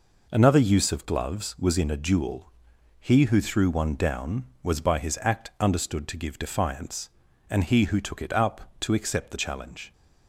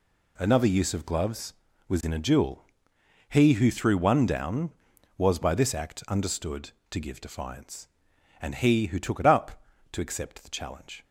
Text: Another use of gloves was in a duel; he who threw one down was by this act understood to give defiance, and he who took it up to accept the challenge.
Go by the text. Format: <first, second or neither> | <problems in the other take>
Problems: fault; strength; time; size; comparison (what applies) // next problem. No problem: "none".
second | says "his" for "this"; at 4.9 s